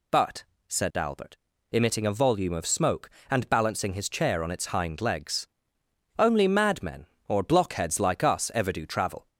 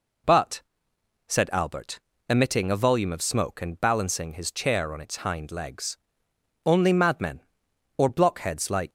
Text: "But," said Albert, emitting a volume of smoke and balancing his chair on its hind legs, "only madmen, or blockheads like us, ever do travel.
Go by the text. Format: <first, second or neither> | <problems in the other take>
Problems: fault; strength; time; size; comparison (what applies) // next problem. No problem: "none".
first | stops before "us ever do travel"; at 8.8 s